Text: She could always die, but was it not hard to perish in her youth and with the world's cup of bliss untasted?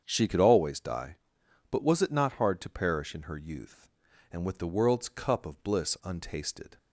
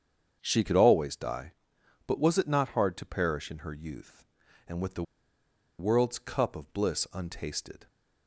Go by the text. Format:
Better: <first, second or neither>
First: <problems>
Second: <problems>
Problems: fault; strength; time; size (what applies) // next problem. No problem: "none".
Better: first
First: starts louder than the rest; strong; until 1.0 s; 7.5 dB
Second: starts louder than the rest; strong; until 1.4 s; 7.5 dB // pauses between "the" and "world's"; noticeable; at 5.0 s; 0.76 s long